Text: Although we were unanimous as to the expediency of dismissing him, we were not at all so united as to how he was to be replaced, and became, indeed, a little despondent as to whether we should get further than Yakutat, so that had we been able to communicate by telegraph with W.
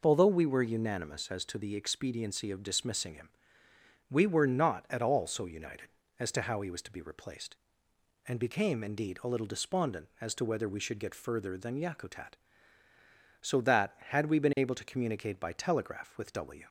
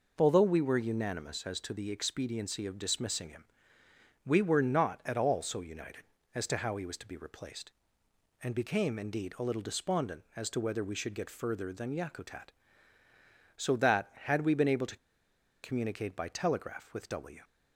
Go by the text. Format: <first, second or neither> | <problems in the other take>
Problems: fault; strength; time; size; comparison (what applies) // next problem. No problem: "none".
first | pauses between "to" and "communicate"; noticeable; at 14.9 s; 0.67 s long